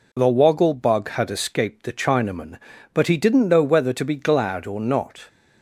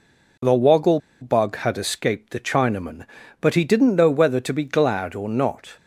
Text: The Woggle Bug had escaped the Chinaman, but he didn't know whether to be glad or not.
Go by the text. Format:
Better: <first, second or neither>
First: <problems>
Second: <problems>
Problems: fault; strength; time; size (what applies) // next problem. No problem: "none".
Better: first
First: none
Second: pauses between "Woggle" and "Bug"; slight; at 0.9 s; 0.21 s long